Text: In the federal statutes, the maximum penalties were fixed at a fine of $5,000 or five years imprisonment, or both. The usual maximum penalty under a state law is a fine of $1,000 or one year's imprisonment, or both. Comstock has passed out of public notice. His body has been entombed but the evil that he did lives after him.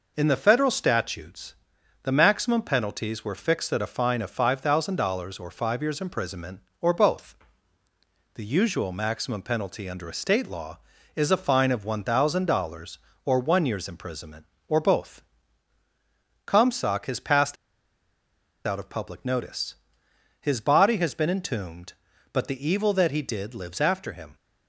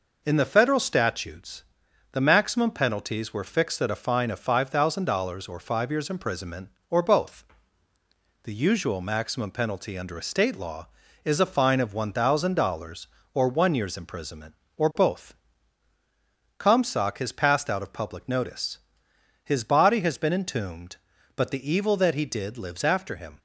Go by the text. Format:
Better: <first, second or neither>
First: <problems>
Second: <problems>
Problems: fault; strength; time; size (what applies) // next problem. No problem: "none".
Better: second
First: pauses between "passed" and "out"; at 17.5 s; 1.1 s long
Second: none